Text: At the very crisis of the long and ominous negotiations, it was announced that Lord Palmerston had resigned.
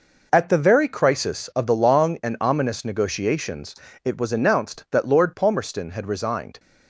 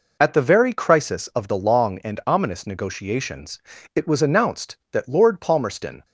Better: first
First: none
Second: stops before "had resigned"; at 6.0 s

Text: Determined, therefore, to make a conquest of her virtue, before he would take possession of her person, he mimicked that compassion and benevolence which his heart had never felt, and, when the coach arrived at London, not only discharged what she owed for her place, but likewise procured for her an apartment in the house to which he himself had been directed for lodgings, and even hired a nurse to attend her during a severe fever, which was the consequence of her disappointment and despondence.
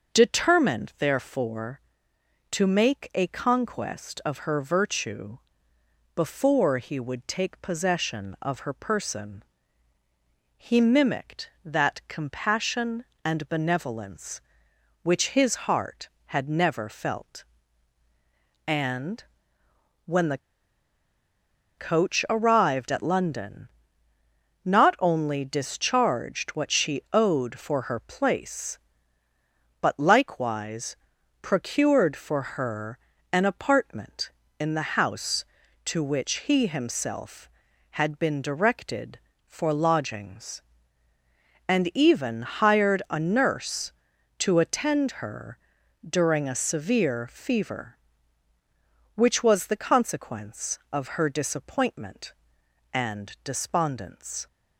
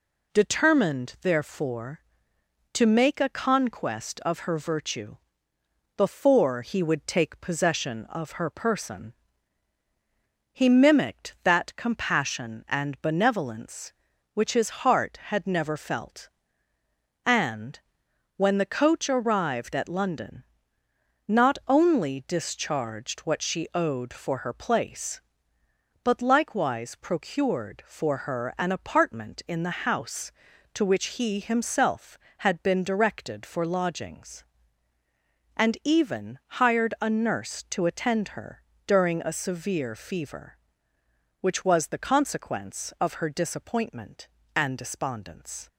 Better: second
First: starts louder than the rest; until 1.1 s; 6.5 dB // pauses between "the" and "coach"; strong; at 20.3 s; 1.4 s long // pauses between "likewise" and "procured"; at 30.9 s; 0.44 s long // pauses between "her" and "an"; slight; at 32.9 s; 0.34 s long // pauses between "her" and "during"; noticeable; at 45.5 s; 0.52 s long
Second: pauses between "her" and "during"; slight; at 38.6 s; 0.24 s long

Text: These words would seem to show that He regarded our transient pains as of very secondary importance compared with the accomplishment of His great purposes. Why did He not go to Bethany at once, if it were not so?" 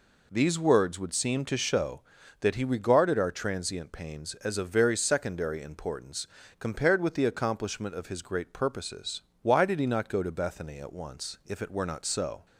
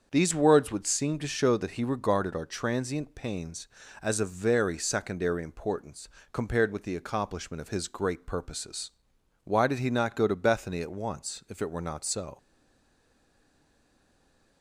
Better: first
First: pauses between "importance" and "compared"; slight; at 6.2 s; 0.32 s long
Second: starts louder than the rest; until 1.1 s; 7 dB // pauses between "importance" and "compared"; slight; at 6.0 s; 0.24 s long // stays silent after the last word; from 12.3 s on; 2.3 s long

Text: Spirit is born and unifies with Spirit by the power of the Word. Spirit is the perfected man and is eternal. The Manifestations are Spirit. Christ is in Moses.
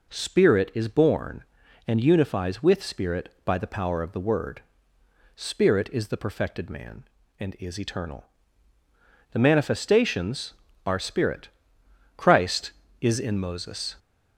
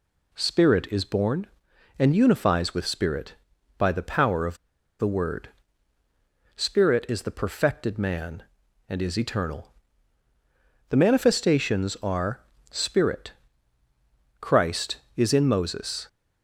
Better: first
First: none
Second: pauses between "of" and "the"; at 4.5 s; 0.42 s long // pauses between "are" and "Spirit"; slight; at 12.3 s; 0.30 s long

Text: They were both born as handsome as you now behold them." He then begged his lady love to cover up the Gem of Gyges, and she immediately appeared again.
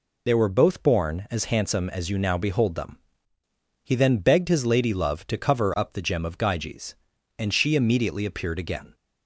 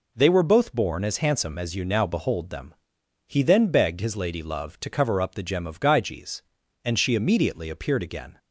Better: second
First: loses the start of "They"; at 0.2 s; 40 ms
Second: none

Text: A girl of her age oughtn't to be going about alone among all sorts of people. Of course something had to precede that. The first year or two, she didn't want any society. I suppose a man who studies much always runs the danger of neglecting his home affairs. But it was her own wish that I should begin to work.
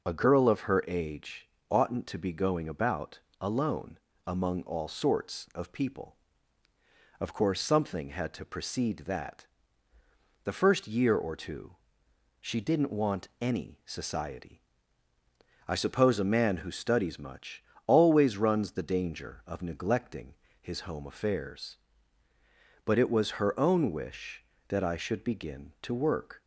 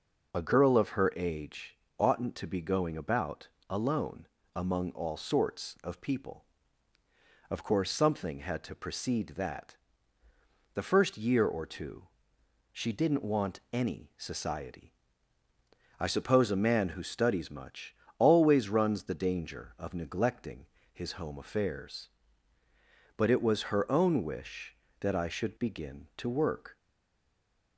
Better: first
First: pauses between "age" and "oughtn't"; slight; at 1.4 s; 0.22 s long // pauses between "about" and "alone"; slight; at 3.2 s; 0.20 s long // pauses between "alone" and "among"; slight; at 3.9 s; 0.28 s long // pauses between "much" and "always"; slight; at 17.6 s; 0.24 s long // pauses between "neglecting" and "his"; slight; at 20.3 s; 0.26 s long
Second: pauses between "age" and "oughtn't"; slight; at 1.7 s; 0.22 s long // pauses between "about" and "alone"; slight; at 3.4 s; 0.20 s long // pauses between "alone" and "among"; slight; at 4.2 s; 0.28 s long // pauses between "much" and "always"; slight; at 17.9 s; 0.24 s long // pauses between "neglecting" and "his"; slight; at 20.6 s; 0.26 s long // stays silent after the last word; from 26.7 s on; 1.0 s long

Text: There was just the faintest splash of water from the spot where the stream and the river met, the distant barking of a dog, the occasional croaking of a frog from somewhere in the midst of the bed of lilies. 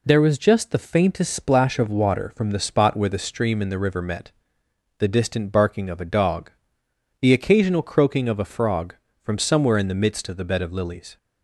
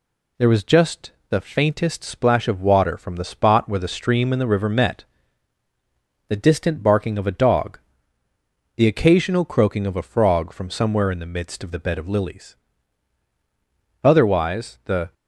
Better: first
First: none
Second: pauses between "just" and "the"; slight; at 1.1 s; 0.18 s long // goes on to say "Otherwise the"; noticeable; from 14.0 s on; 1.1 s long

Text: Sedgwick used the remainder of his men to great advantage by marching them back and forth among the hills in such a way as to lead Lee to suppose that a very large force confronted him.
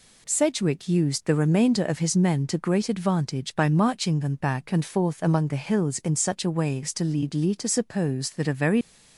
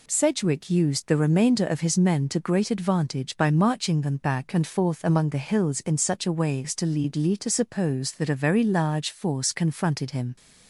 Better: second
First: stops before "large force confronted him"; at 8.8 s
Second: none

